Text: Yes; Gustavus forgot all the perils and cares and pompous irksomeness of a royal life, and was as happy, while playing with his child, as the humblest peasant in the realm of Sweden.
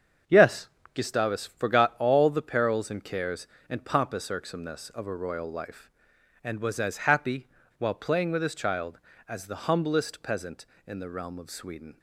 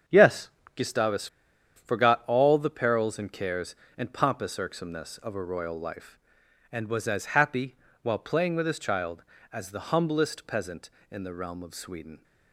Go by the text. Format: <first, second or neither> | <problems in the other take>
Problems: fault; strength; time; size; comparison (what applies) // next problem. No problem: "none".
first | starts louder than the rest; strong; until 1.8 s; 7 dB; strong in the first // pauses between "Gustavus" and "forgot"; noticeable; at 1.2 s; 0.49 s long